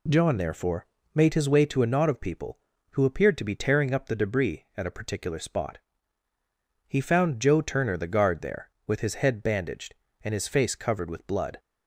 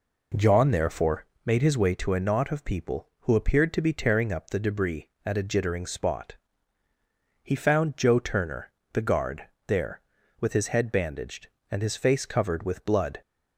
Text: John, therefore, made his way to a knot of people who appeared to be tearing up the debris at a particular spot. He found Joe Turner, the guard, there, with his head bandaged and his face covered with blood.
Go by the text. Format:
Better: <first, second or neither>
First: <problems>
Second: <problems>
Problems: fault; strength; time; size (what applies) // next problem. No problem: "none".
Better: first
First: none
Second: says "jittering" for "particular"; at 5.4 s